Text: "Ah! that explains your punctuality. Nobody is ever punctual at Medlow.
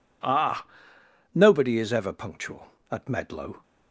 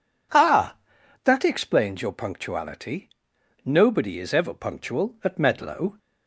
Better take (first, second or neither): second